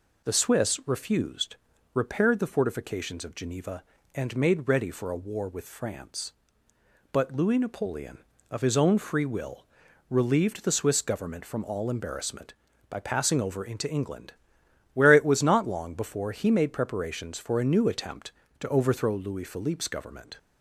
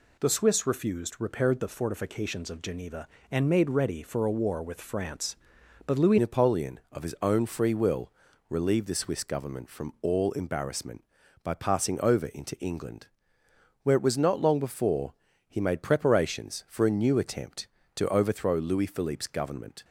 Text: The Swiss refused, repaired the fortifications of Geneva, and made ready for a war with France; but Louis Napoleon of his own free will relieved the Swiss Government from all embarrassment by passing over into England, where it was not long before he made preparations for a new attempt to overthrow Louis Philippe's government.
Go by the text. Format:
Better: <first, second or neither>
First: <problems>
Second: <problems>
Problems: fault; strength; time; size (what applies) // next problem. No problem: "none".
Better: first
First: pauses between "will" and "relieved"; at 9.6 s; 0.44 s long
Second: changes voice at "Napoleon"; from 6.1 s on; 13.7 s long // pauses between "will" and "relieved"; slight; at 8.1 s; 0.36 s long // pauses between "before" and "he"; slight; at 15.1 s; 0.34 s long